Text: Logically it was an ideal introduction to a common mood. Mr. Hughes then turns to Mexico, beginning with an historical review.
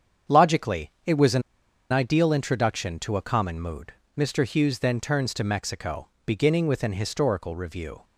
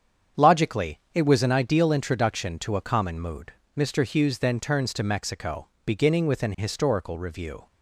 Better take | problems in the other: second | starts louder than the rest; strong; until 1.9 s; 7.5 dB; strong in the second // pauses between "an" and "ideal"; noticeable; at 1.4 s; 0.49 s long

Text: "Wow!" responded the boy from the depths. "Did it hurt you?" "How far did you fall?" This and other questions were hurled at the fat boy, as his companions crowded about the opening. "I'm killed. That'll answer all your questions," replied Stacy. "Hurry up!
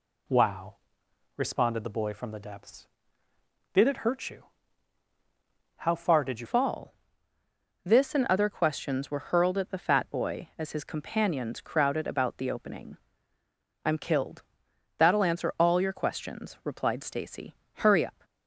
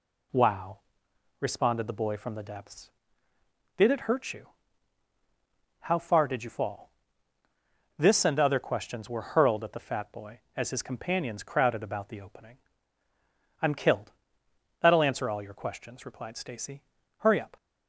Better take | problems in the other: second | changes voice at "fall"; from 6.4 s on; 11.8 s long

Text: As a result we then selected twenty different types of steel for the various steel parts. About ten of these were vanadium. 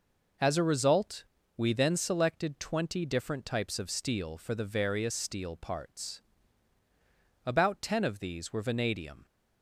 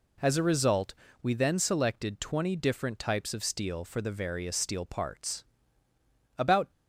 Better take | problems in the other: first | pauses between "result" and "we"; slight; at 0.9 s; 0.28 s long; slight in the first // stops before "ten of these were vanadium"; at 6.7 s

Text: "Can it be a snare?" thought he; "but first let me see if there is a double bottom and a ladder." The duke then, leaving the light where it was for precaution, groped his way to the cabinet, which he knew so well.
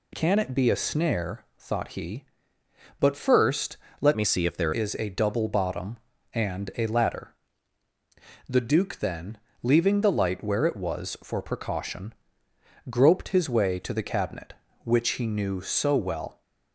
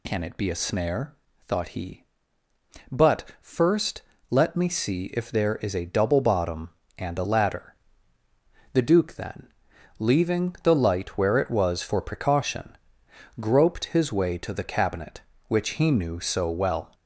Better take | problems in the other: second | pauses between "first" and "let"; slight; at 3.7 s; 0.22 s long; slight in the second // changes voice from "me" to "there"; from 4.1 to 4.7 s; 0.6 s long

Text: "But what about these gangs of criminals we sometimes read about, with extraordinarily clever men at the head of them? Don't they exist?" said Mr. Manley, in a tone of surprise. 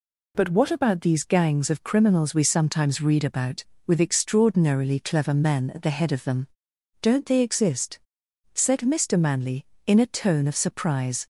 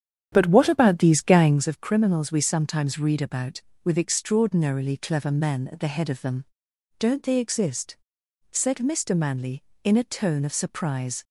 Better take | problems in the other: first | starts louder than the rest; strong; until 1.7 s; 9 dB

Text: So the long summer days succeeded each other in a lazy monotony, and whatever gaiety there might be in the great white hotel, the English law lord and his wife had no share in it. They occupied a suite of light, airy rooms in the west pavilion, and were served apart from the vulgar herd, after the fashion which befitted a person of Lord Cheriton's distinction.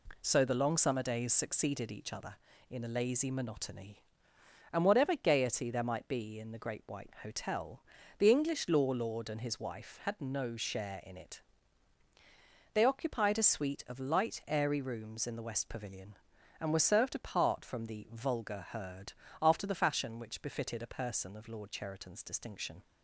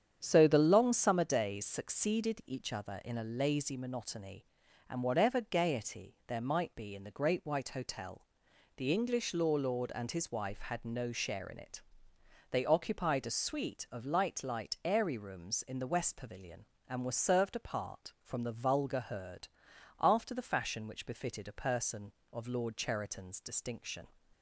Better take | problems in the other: first | starts louder than the rest; strong; until 1.2 s; 8.5 dB // says "light" twice; at 14.4 s

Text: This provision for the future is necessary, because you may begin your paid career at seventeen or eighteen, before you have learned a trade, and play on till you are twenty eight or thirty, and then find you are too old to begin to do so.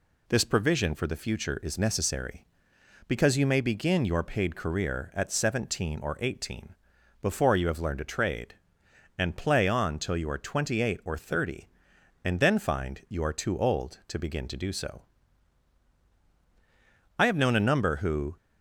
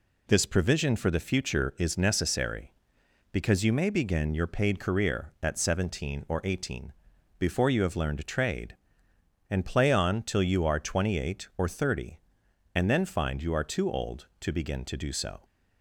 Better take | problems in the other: second | goes on to say "I have known a number who"; noticeable; from 17.1 s on; 1.1 s long

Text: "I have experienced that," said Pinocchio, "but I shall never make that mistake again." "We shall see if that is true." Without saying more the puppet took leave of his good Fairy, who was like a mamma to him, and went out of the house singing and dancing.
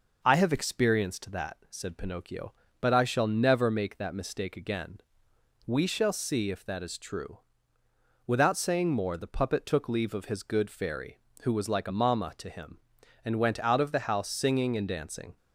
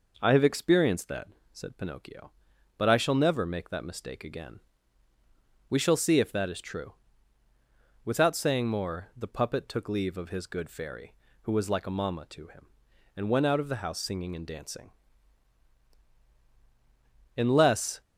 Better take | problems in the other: first | goes on to say "In less"; noticeable; from 17.3 s on; 0.66 s long

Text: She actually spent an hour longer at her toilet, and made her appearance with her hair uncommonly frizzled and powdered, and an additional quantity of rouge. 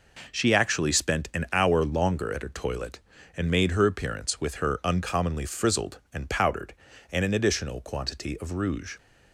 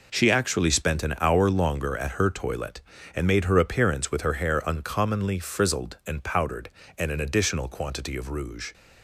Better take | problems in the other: second | skips "hair"; at 4.8 s

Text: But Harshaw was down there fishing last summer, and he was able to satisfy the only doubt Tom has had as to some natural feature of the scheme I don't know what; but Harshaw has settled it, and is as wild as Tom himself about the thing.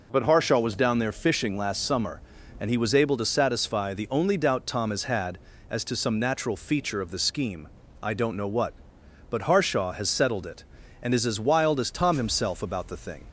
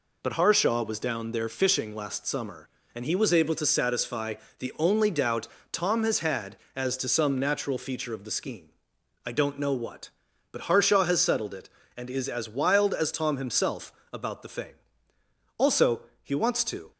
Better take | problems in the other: first | pauses between "satisfy" and "the"; slight; at 4.3 s; 0.24 s long // pauses between "doubt" and "Tom"; slight; at 5.4 s; 0.24 s long // pauses between "scheme" and "I"; noticeable; at 8.6 s; 0.56 s long; slight in the first // pauses between "himself" and "about"; slight; at 13.9 s; 0.22 s long // goes on to say "Also he wants to"; from 15.5 s on; 1.3 s long

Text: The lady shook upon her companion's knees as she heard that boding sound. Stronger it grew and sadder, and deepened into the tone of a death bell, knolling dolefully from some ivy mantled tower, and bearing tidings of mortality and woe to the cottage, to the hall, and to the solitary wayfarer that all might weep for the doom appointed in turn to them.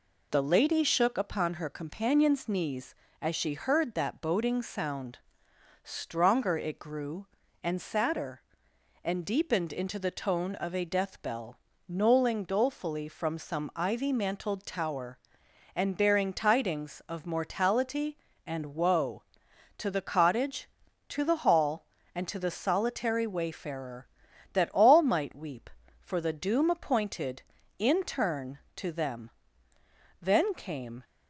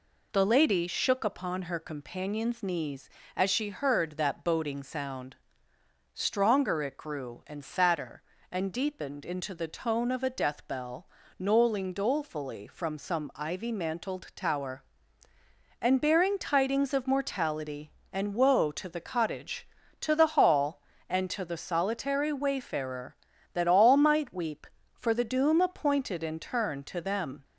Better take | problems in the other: second | goes on to say "Then came"; noticeable; from 30.2 s on; 0.82 s long

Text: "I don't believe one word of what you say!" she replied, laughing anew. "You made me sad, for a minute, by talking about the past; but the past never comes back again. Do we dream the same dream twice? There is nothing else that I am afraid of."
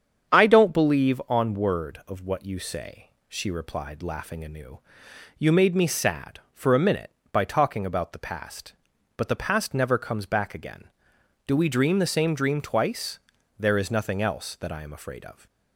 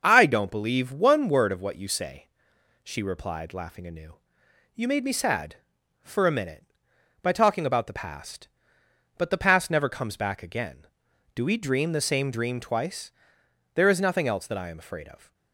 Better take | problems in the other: second | starts louder than the rest; strong; until 1.3 s; 8 dB; also in the second // says "on" for "one"; at 1.2 s

